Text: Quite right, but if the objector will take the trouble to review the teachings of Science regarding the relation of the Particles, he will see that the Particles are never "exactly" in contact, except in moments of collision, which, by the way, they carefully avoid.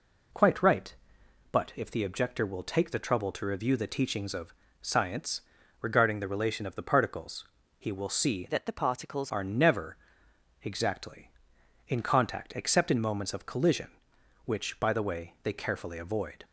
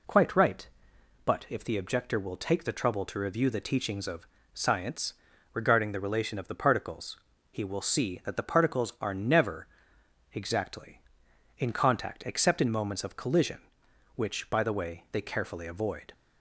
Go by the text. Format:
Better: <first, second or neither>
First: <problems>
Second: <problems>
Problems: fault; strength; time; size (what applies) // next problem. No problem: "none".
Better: second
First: pauses between "of" and "Science"; slight; at 4.5 s; 0.30 s long // pauses between "Science" and "regarding"; at 5.4 s; 0.38 s long // changes voice from "that" to "Particles"; from 8.4 to 9.3 s; 0.9 s long // pauses between "never" and "exactly"; noticeable; at 9.9 s; 0.66 s long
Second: pauses between "of" and "Science"; slight; at 4.2 s; 0.28 s long // pauses between "Science" and "regarding"; at 5.1 s; 0.38 s long // pauses between "never" and "exactly"; noticeable; at 9.6 s; 0.66 s long